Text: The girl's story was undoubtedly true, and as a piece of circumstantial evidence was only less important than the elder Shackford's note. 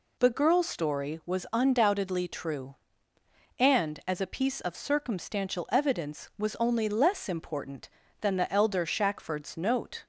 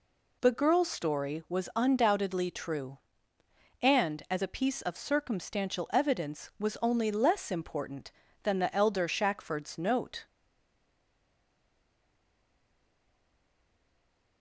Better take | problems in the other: first | stays silent after the last word; strong; from 10.2 s on; 4.2 s long

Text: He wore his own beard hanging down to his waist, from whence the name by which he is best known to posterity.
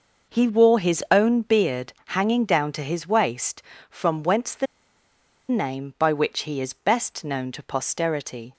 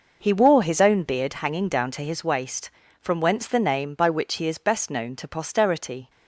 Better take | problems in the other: second | pauses between "the" and "name"; noticeable; at 4.6 s; 0.83 s long

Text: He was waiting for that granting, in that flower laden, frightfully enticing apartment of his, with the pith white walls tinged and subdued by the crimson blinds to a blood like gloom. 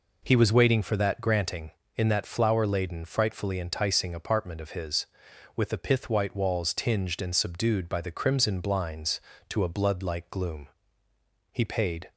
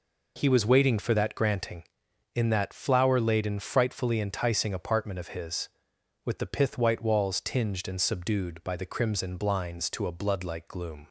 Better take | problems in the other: second | goes on to say "He paid"; from 11.5 s on; 0.60 s long

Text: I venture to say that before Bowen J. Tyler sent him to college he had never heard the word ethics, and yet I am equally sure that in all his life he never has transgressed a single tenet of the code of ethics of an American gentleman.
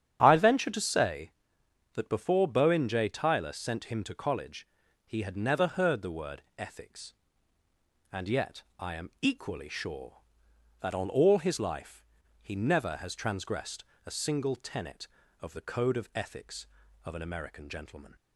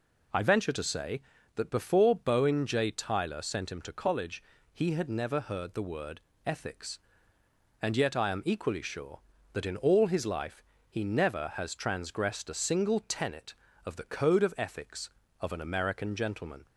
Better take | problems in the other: second | starts louder than the rest; strong; until 1.2 s; 9 dB // pauses between "college" and "he"; at 4.6 s; 0.40 s long; slight in the second // pauses between "word" and "ethics"; slight; at 6.4 s; 0.16 s long; slight in the second // pauses between "yet" and "I"; slight; at 8.6 s; 0.18 s long // says "on" for "in"; at 10.9 s // pauses between "life" and "he"; at 12.0 s; 0.36 s long; slight in the second // pauses between "transgressed" and "a"; slight; at 13.8 s; 0.22 s long

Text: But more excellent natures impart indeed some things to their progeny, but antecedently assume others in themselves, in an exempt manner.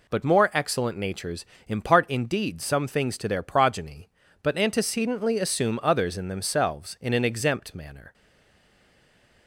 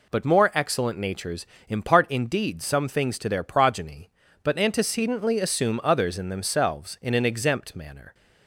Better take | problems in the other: second | pauses between "natures" and "impart"; slight; at 1.4 s; 0.22 s long; slight in the second // stays silent after the last word; noticeable; from 8.1 s on; 1.3 s long

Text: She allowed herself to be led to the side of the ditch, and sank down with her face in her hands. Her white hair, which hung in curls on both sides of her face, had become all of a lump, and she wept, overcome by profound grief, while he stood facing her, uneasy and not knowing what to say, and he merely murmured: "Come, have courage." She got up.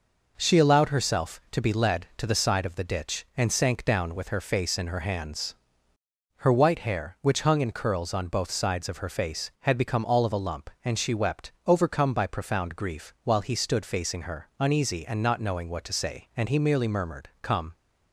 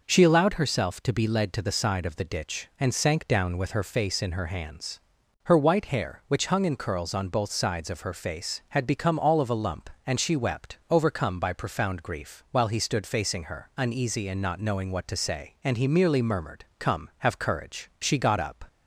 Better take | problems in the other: second | stops before "have courage She got up"; at 17.7 s

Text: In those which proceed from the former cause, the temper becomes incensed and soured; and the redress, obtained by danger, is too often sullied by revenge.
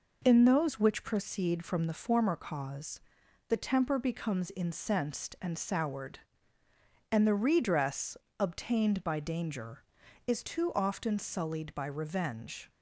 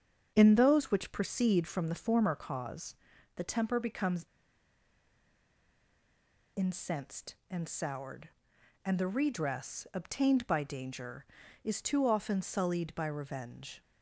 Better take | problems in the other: first | starts louder than the rest; until 1.3 s; 7 dB // pauses between "becomes" and "incensed"; strong; at 4.2 s; 2.3 s long

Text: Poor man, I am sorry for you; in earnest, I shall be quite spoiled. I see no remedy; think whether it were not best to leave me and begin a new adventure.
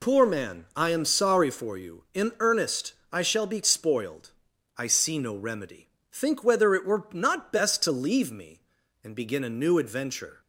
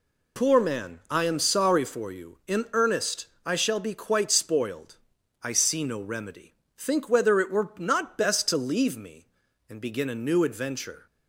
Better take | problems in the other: second | skips "quite"; at 3.6 s

